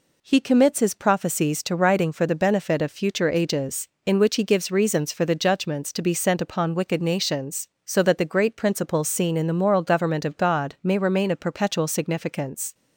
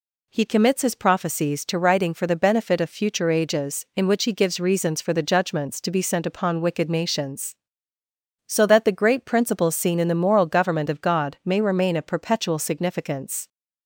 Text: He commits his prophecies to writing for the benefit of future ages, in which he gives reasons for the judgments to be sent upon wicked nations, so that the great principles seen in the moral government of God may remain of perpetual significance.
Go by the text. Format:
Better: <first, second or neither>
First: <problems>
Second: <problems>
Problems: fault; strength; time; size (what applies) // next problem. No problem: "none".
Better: neither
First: none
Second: none